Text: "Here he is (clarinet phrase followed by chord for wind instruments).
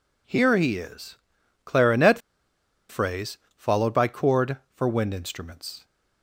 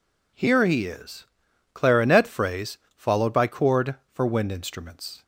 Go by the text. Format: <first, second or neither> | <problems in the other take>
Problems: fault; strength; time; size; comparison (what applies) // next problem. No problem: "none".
second | pauses between "clarinet" and "phrase"; noticeable; at 2.1 s; 0.70 s long // pauses between "phrase" and "followed"; slight; at 3.3 s; 0.18 s long; slight in the second